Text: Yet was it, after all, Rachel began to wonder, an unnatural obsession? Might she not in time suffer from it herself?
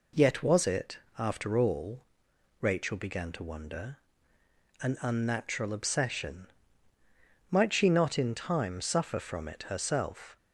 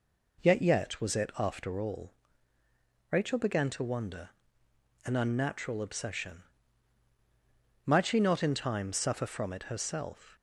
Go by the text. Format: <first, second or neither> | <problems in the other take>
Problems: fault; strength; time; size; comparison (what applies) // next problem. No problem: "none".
first | says "Yet" twice; at 0.6 s